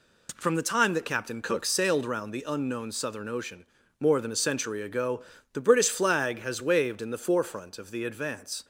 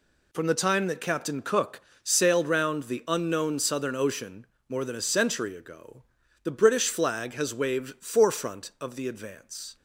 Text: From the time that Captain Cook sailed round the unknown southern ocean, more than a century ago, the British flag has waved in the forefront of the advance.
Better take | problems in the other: first | pauses between "Cook" and "sailed"; slight; at 1.8 s; 0.22 s long // skips "in the"; at 8.0 s

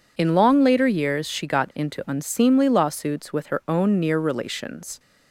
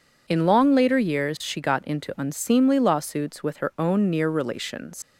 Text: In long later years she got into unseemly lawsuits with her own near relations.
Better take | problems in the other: first | leaves "relations" unfinished; at 5.0 s; 75 ms

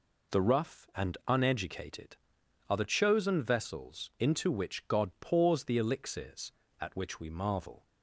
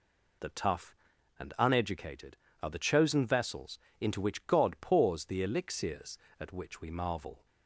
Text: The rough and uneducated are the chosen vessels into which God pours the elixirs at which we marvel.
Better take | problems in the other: first | says "tough" for "rough"; at 0.4 s // pauses between "vessels" and "into"; slight; at 3.7 s; 0.22 s long

